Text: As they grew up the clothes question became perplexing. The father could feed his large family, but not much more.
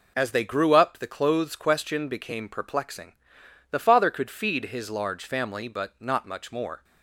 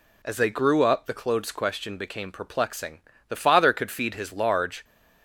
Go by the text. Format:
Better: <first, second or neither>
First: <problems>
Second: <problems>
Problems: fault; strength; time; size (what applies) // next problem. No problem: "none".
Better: first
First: none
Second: stops before "family but not much more"; at 4.8 s